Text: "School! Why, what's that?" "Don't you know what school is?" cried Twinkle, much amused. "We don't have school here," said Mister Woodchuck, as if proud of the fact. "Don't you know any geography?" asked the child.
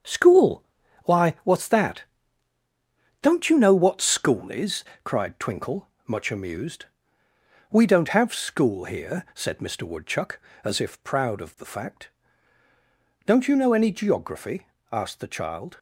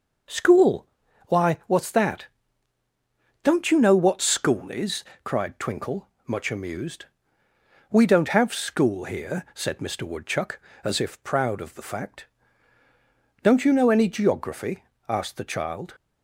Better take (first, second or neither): second